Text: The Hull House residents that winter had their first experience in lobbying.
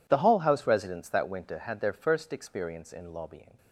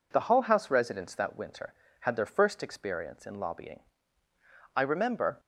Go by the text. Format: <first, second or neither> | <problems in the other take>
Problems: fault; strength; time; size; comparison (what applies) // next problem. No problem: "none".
first | goes on to say "I remember"; noticeable; from 4.7 s on; 0.64 s long